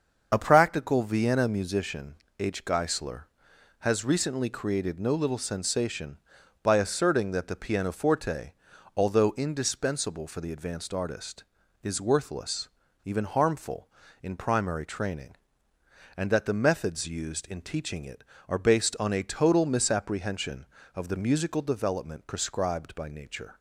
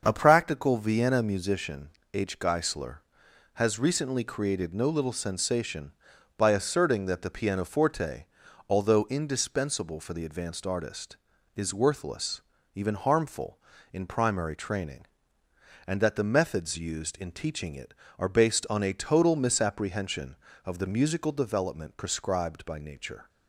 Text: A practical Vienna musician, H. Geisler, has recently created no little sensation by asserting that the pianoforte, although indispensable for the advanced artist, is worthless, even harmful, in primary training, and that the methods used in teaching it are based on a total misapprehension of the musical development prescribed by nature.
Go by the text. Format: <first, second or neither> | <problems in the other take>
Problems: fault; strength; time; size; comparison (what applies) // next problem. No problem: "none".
second | loses the start of "A"; at 0.3 s; 35 ms // starts louder than the rest; until 1.3 s; 6.5 dB; also in the second